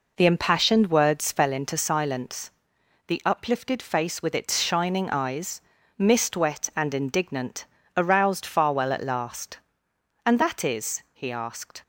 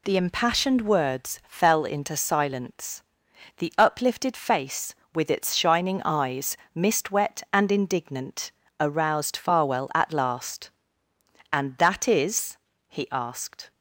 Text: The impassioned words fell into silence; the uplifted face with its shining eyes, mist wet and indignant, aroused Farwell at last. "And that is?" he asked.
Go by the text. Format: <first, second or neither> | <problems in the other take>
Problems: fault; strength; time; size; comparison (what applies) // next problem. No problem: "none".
neither | none